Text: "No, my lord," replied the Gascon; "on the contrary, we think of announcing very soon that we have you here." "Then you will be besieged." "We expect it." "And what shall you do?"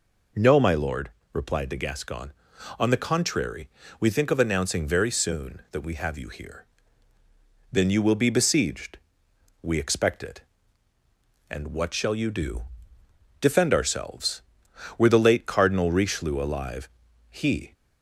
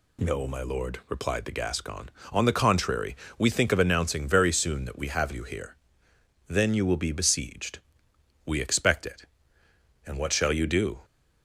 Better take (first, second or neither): second